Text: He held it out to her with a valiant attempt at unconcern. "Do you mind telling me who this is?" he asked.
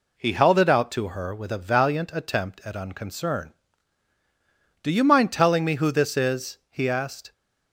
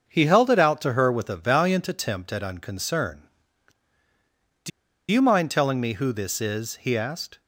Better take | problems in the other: first | starts louder than the rest; until 1.0 s; 6.5 dB // pauses between "Do" and "you"; at 4.7 s; 0.41 s long

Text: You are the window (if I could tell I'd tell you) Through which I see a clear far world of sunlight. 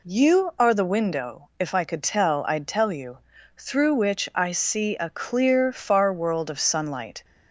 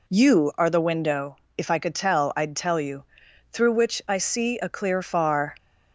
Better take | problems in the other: first | stops before "world of sunlight"; at 5.5 s

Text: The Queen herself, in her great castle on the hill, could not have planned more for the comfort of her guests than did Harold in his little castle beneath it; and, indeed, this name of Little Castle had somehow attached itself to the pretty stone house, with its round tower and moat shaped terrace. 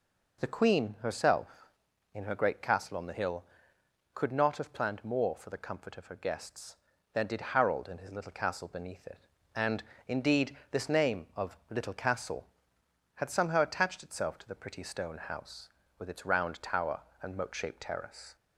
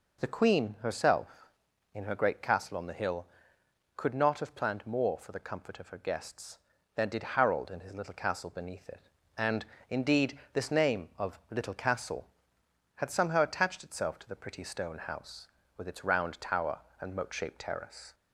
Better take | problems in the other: neither | none

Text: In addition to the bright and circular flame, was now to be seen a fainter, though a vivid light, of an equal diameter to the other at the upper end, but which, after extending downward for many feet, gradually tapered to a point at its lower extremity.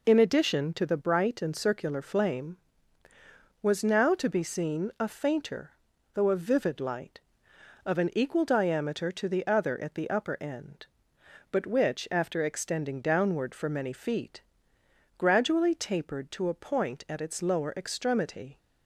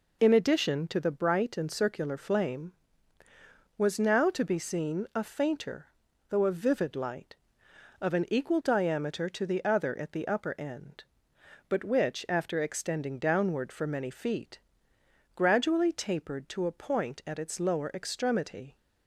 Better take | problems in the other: neither | none

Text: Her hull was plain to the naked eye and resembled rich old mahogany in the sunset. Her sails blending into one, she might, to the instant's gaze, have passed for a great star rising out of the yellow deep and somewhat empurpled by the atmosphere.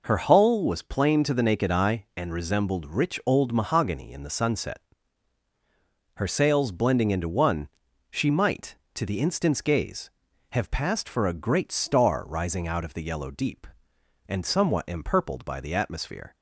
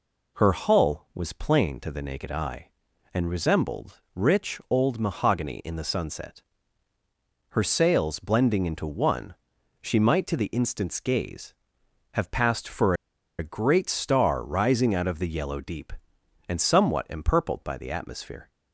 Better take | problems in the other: first | pauses between "for" and "a"; at 12.9 s; 0.45 s long

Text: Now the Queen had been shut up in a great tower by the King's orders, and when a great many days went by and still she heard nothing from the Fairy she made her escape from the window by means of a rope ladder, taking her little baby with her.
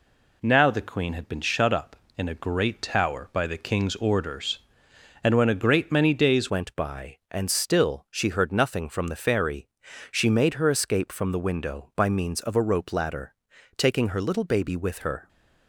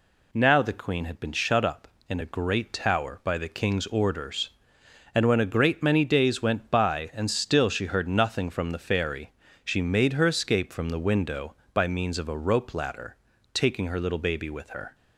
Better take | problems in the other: second | changes voice at "went"; from 6.4 s on; 8.8 s long // pauses between "Fairy" and "she"; at 9.6 s; 0.44 s long; slight in the second

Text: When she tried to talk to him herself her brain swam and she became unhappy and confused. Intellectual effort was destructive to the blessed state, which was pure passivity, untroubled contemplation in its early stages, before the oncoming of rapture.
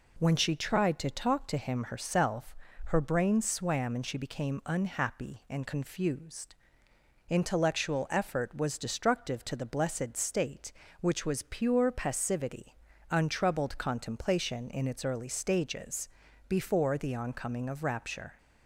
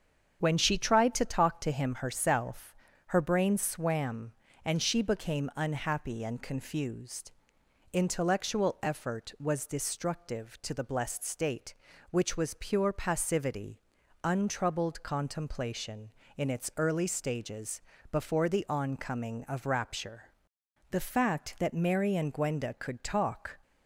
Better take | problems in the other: first | starts louder than the rest; strong; until 1.4 s; 7.5 dB // pauses between "herself" and "her"; slight; at 2.7 s; 0.36 s long; slight in the first // goes on to say "The fact that Mary and Gwenda could talk"; strong; from 20.9 s on; 2.6 s long

